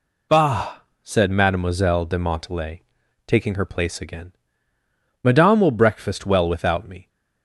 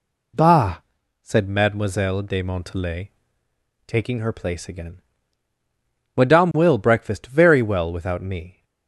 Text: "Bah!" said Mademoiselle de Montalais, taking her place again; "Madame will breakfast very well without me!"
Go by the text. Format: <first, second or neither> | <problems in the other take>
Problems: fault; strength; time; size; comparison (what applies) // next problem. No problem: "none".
second | skips "very"; at 6.2 s